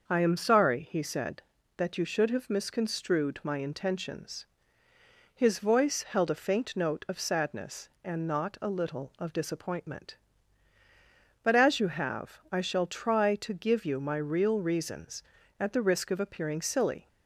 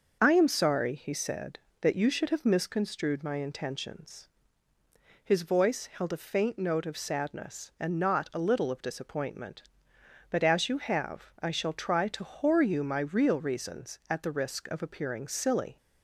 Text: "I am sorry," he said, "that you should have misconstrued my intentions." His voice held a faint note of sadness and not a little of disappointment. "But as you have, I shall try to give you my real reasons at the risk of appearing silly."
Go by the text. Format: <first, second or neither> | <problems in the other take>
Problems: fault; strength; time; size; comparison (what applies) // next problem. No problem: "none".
first | starts louder than the rest; noticeable; until 1.2 s; 6 dB; noticeable in the first // says "whore" for "give"; at 12.2 s